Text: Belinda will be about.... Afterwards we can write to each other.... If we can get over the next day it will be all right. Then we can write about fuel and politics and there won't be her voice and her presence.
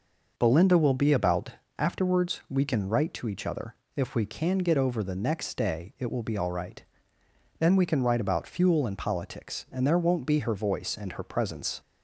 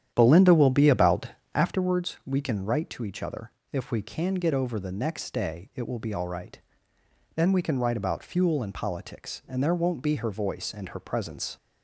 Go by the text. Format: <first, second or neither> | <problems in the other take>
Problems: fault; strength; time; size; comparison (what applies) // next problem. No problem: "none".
first | starts louder than the rest; strong; until 1.9 s; 10 dB